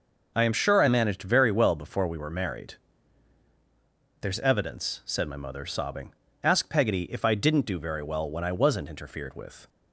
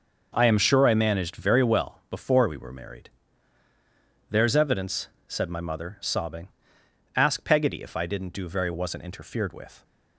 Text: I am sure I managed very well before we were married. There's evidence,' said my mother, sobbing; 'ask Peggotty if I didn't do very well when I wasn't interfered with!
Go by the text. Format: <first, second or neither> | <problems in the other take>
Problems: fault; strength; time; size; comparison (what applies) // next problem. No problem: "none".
first | skips "well when I"; at 8.7 s